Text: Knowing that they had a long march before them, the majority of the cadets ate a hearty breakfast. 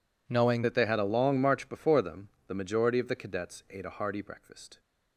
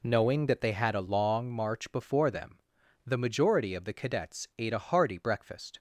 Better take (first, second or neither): second